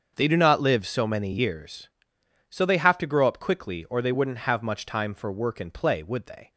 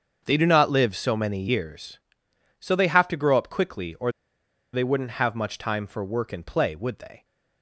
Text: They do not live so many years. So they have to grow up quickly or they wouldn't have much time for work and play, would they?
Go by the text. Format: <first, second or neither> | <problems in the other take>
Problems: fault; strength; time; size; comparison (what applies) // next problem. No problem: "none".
first | starts louder than the rest; until 1.2 s; 7 dB; also in the first // pauses between "or" and "they"; noticeable; at 4.1 s; 0.62 s long